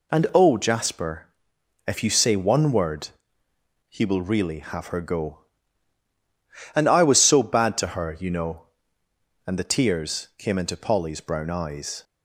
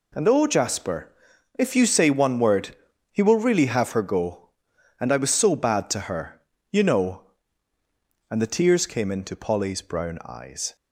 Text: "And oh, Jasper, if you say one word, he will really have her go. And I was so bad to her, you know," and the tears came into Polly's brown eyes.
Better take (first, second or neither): neither